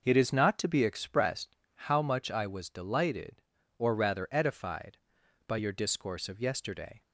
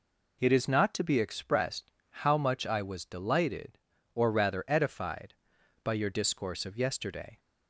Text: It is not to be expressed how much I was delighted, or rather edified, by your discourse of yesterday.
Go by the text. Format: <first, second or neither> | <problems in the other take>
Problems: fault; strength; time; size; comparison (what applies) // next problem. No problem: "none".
second | starts louder than the rest; noticeable; until 1.5 s; 5.5 dB // pauses between "expressed" and "how"; slight; at 1.5 s; 0.18 s long; slight in the second